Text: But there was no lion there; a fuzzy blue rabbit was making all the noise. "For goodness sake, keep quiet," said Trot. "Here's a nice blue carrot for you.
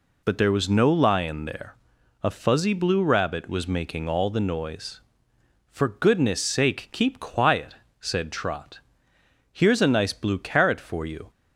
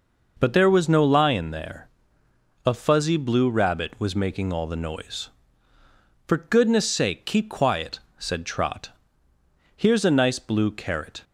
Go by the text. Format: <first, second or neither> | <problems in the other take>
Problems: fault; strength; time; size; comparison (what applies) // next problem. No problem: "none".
first | stops before "for you"; at 11.2 s